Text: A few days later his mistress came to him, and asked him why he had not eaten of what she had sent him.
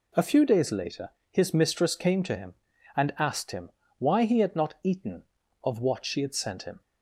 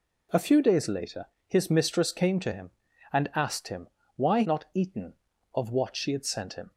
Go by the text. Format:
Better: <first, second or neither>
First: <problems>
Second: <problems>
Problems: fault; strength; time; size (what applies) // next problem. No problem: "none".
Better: first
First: pauses between "later" and "his"; slight; at 1.0 s; 0.22 s long // pauses between "him" and "why"; slight; at 3.6 s; 0.28 s long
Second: pauses between "later" and "his"; slight; at 1.2 s; 0.22 s long // pauses between "him" and "why"; slight; at 3.8 s; 0.28 s long // skips "he had"; at 4.4 s